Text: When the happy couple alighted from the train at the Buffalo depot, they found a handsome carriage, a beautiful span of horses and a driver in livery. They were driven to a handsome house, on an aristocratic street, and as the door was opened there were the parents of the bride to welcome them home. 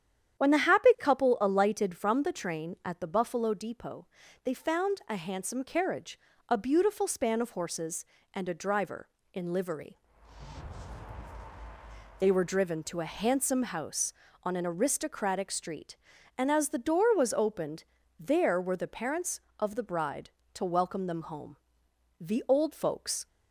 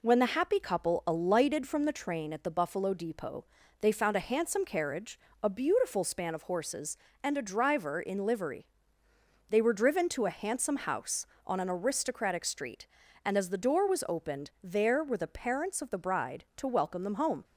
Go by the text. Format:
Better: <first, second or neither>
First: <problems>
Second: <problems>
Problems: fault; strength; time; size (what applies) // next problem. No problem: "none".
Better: second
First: starts louder than the rest; strong; until 1.4 s; 9.5 dB // pauses between "opened" and "there"; slight; at 17.8 s; 0.34 s long // goes on to say "The old folks"; noticeable; from 22.1 s on; 1.0 s long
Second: none